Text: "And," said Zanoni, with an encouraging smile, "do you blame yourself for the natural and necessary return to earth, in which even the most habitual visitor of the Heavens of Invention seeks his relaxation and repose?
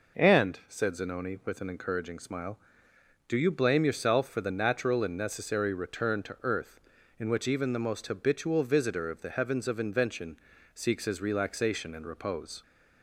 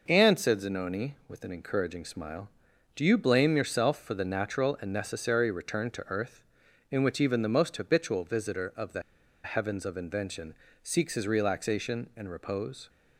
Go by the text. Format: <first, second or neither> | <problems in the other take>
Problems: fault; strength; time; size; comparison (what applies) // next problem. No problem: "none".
first | pauses between "the" and "Heavens"; at 9.0 s; 0.42 s long // pauses between "Invention" and "seeks"; slight; at 10.5 s; 0.28 s long; slight in the first